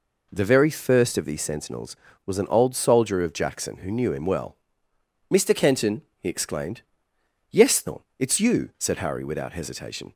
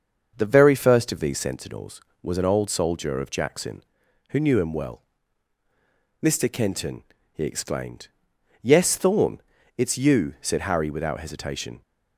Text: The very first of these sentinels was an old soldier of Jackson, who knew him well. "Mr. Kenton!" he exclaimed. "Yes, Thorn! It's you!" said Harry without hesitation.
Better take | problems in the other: first | starts louder than the rest; until 1.6 s; 6.5 dB

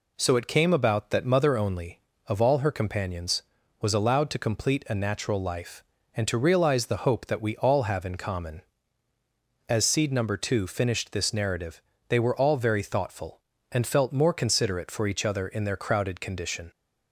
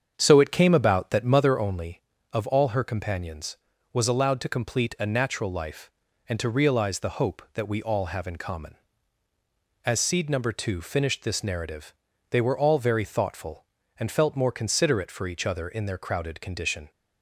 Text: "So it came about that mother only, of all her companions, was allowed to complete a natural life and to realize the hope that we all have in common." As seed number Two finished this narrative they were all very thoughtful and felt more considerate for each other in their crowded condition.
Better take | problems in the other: first | starts louder than the rest; strong; until 1.6 s; 7.5 dB // pauses between "narrative" and "they"; at 11.9 s; 0.38 s long; slight in the first

